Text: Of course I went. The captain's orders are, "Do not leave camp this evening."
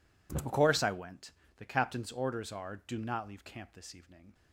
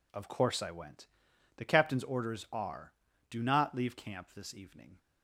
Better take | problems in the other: neither | none

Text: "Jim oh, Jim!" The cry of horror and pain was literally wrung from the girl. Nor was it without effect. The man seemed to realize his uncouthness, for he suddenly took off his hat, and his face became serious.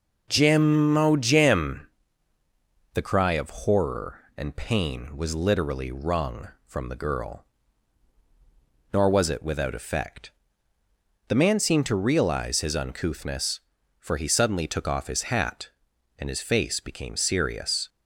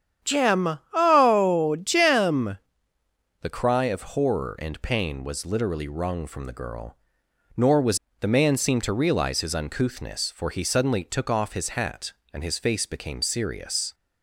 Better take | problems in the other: first | starts louder than the rest; strong; until 1.3 s; 9 dB // skips "it without effect"; at 8.0 s

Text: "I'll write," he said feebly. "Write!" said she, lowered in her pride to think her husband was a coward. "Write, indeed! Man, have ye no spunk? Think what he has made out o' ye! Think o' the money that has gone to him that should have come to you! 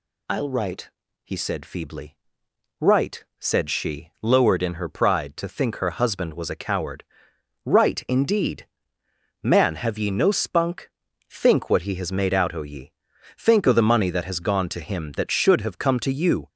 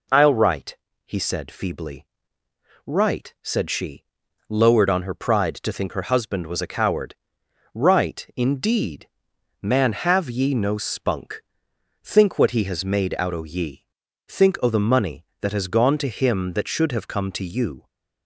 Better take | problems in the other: first | says "on" for "in"; at 4.8 s

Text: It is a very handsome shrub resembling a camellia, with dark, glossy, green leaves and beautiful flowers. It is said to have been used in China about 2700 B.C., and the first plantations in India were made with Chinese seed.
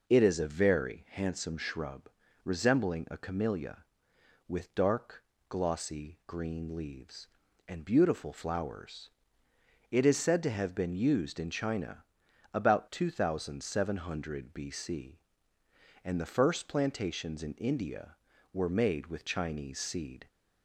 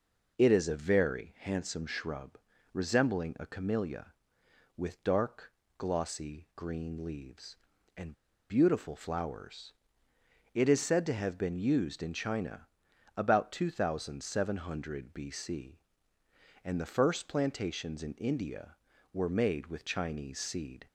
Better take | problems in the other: first | pauses between "shrub" and "resembling"; slight; at 2.3 s; 0.36 s long; slight in the first // pauses between "and" and "beautiful"; at 8.1 s; 0.37 s long // pauses between "China" and "about"; noticeable; at 12.6 s; 0.50 s long; noticeable in the first

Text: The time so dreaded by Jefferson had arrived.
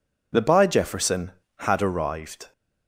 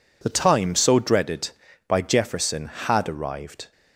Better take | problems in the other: second | skips "time so dreaded"; at 0.4 s

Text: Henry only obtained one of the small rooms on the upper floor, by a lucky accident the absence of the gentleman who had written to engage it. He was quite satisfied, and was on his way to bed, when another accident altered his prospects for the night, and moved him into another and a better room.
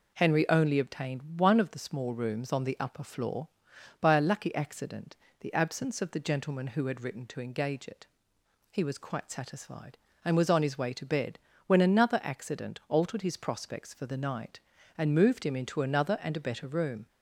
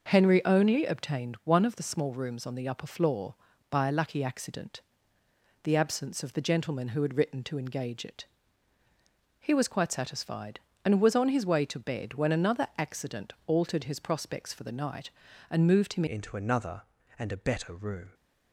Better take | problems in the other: first | pauses between "accident" and "the"; noticeable; at 4.8 s; 0.84 s long; slight in the first // changes voice at "into"; from 16.0 s on; 2.1 s long

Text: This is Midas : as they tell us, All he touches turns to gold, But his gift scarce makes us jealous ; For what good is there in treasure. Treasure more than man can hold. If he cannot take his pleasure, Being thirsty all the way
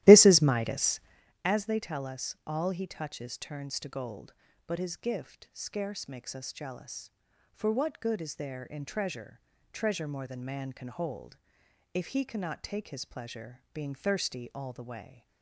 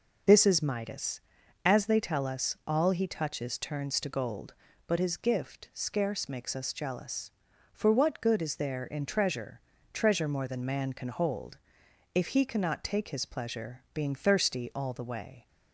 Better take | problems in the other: second | starts louder than the rest; strong; until 1.3 s; 15 dB

